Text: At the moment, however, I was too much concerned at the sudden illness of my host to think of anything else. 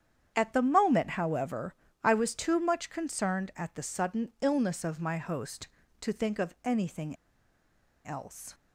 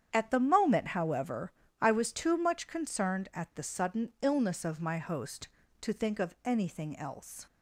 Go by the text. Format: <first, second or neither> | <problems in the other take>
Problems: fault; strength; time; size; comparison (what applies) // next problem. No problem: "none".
second | starts louder than the rest; strong; until 1.3 s; 8.5 dB; strong in the second // pauses between "anything" and "else"; noticeable; at 7.1 s; 0.90 s long